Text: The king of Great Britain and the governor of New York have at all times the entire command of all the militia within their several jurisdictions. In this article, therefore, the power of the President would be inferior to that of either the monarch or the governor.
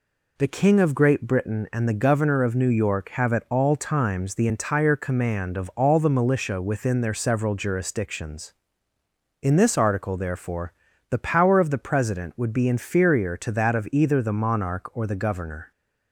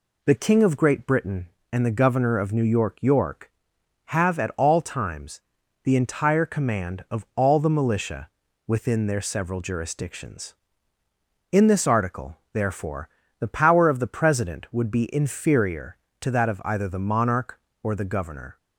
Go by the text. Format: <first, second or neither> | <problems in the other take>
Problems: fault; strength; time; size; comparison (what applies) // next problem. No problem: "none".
first | says "York" twice; at 3.0 s // pauses between "times" and "the"; at 5.4 s; 0.42 s long // pauses between "militia" and "within"; at 8.2 s; 0.40 s long